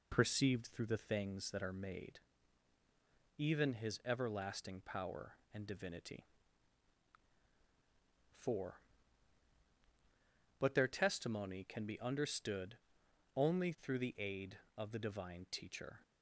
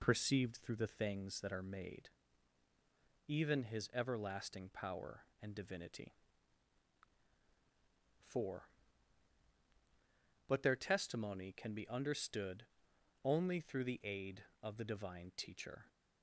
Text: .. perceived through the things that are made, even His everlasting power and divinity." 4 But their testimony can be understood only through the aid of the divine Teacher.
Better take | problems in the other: neither | pauses between "understood" and "only"; noticeable; the same in both

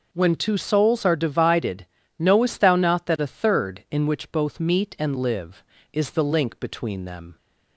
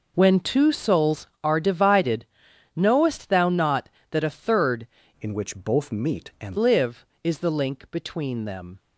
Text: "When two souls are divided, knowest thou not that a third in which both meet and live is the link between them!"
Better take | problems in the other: first | changes voice from "in" to "and"; from 5.2 to 6.5 s; 1.3 s long

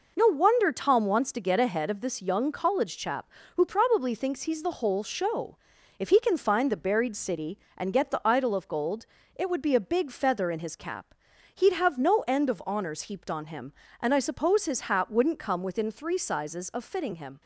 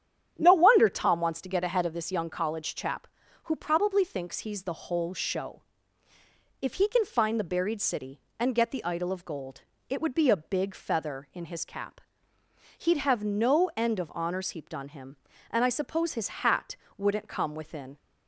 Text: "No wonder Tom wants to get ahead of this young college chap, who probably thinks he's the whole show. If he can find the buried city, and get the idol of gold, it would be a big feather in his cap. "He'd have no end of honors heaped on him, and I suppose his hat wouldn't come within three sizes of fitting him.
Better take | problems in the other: first | starts louder than the rest; strong; until 1.3 s; 9.5 dB // pauses between "hat" and "wouldn't"; slight; at 16.7 s; 0.20 s long // stops before "three sizes of fitting him"; at 17.9 s

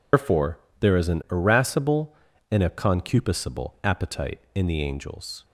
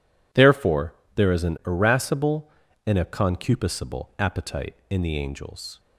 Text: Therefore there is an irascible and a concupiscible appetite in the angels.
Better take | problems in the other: second | loses the start of "Therefore"; at 0.1 s; 150 ms // pauses between "Therefore" and "there"; slight; at 0.5 s; 0.22 s long; slight in the second

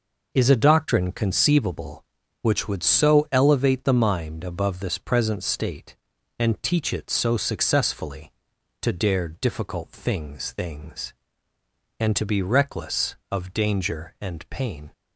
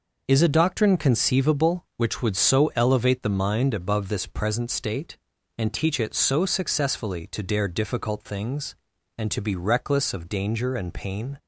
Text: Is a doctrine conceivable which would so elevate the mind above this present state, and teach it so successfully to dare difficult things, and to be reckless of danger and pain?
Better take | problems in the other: second | says "things" twice; at 10.5 s

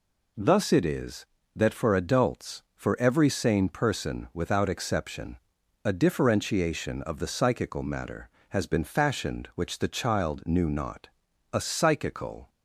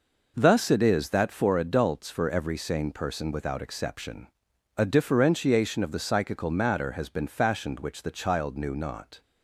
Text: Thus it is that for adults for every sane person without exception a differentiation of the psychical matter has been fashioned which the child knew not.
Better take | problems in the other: second | pauses between "exception" and "a"; noticeable; at 5.3 s; 0.48 s long; noticeable in the second // goes on to say "A psychical"; noticeable; from 11.5 s on; 0.96 s long

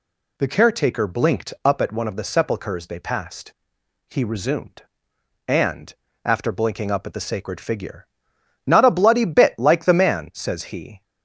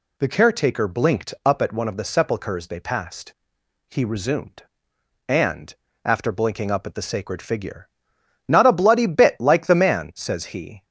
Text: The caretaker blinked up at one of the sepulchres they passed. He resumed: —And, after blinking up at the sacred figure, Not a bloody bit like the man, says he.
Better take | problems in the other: neither | none

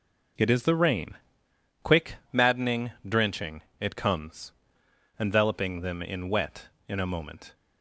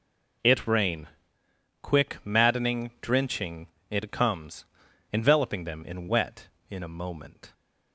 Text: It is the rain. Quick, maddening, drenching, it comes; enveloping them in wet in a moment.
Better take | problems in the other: first | skips "is the"; at 0.6 s

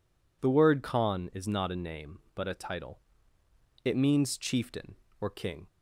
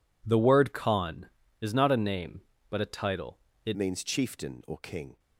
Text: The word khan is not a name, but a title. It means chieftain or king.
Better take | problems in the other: first | changes voice at "means"; from 3.7 s on; 1.4 s long

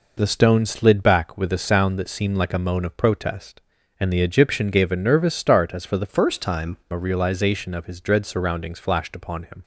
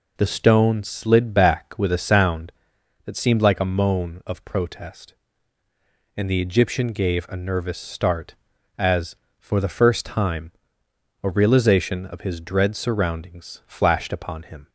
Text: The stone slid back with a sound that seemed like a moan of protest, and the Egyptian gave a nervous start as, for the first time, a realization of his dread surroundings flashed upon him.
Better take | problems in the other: second | changes voice from "first" to "time"; from 6.0 to 6.7 s; 0.7 s long

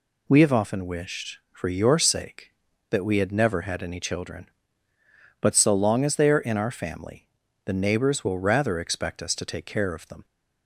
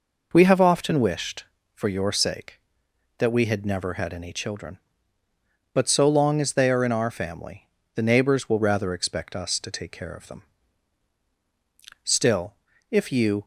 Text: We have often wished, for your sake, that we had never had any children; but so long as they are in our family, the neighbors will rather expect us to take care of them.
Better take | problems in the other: first | goes on to say "Still if you"; from 12.0 s on; 1.4 s long

